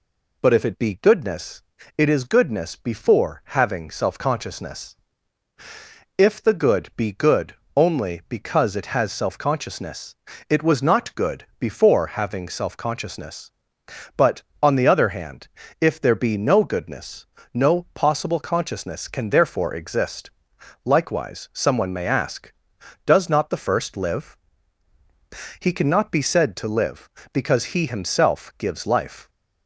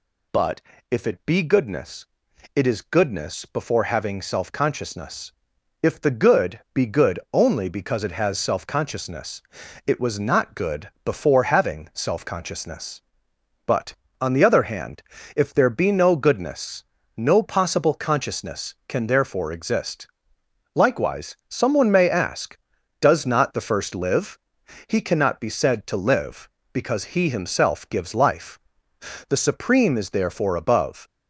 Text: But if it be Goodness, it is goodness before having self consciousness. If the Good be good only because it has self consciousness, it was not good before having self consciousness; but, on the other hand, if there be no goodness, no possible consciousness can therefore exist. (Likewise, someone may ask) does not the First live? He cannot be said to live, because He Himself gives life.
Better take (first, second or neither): first